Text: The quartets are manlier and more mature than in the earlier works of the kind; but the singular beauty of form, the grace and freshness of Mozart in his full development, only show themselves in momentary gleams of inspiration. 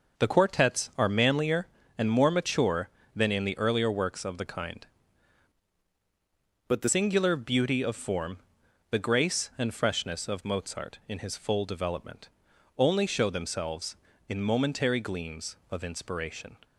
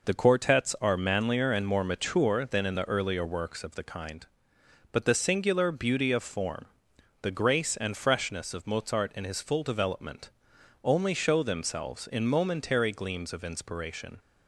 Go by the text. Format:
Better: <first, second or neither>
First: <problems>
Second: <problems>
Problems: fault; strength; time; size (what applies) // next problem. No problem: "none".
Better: second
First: changes voice from "but" to "the"; from 6.6 to 6.8 s; 0.2 s long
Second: none